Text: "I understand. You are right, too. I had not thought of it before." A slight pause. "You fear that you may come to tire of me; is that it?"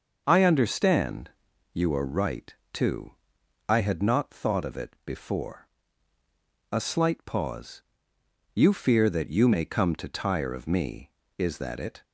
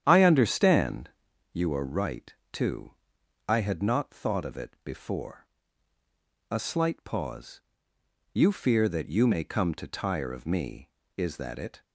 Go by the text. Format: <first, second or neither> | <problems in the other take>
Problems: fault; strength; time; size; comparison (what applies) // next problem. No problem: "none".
first | starts louder than the rest; strong; until 1.2 s; 9.5 dB